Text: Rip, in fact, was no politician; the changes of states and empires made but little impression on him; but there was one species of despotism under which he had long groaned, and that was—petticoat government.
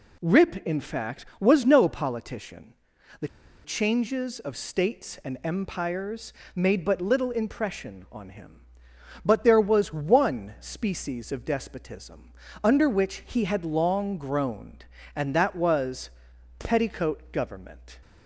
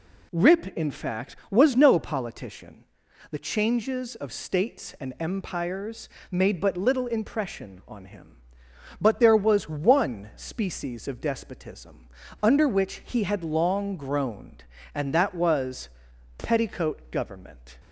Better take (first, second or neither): second